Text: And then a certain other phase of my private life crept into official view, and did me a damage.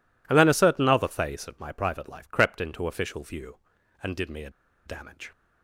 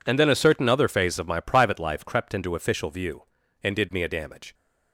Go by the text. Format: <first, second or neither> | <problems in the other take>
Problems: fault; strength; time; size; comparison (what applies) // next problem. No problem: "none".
second | pauses between "a" and "damage"; slight; at 4.4 s; 0.35 s long